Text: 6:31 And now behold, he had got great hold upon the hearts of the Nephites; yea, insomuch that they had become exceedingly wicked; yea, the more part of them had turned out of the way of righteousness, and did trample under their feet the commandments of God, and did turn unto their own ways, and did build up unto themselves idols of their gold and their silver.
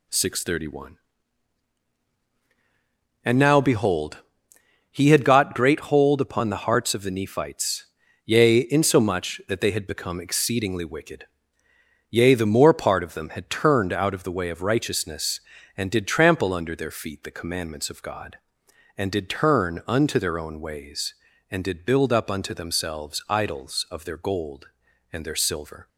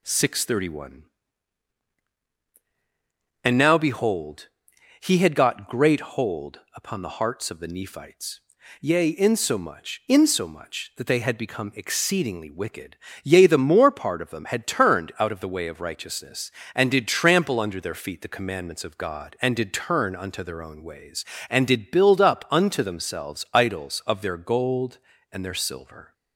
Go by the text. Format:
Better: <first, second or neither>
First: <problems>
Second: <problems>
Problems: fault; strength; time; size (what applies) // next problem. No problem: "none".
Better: first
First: none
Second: pauses between "hold" and "upon"; slight; at 6.5 s; 0.16 s long // says "insomuch" twice; at 10.0 s